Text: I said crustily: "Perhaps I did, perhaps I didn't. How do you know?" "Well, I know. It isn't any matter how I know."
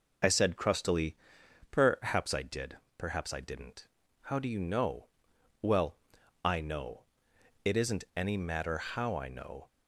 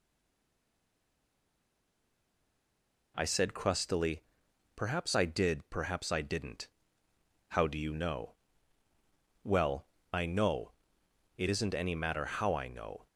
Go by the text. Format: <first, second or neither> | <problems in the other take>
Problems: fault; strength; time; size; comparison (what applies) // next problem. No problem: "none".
first | stays silent before the first word; strong; until 3.1 s; 3.1 s long